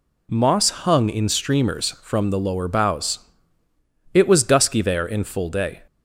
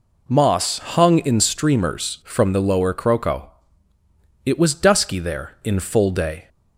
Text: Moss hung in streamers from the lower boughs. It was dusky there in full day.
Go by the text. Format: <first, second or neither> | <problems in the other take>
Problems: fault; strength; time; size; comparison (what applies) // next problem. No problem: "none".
first | says "croco" for "boughs"; at 2.9 s